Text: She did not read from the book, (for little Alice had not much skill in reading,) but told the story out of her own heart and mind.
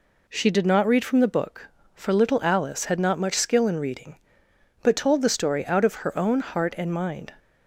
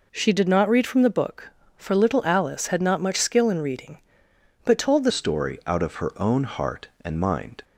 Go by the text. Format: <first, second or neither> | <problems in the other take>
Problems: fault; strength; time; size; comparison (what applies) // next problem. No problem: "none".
first | changes voice at "story"; from 5.1 s on; 2.5 s long